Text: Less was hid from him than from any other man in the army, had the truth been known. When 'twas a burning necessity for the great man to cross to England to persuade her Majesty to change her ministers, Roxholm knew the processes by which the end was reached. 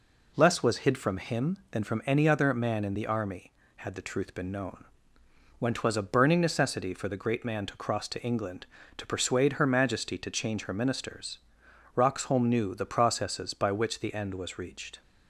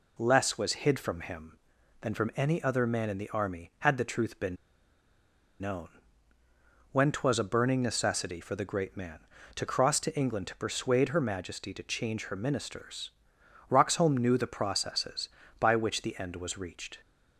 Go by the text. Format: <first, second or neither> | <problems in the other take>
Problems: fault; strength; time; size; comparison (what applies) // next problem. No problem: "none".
first | pauses between "been" and "known"; at 4.5 s; 1.0 s long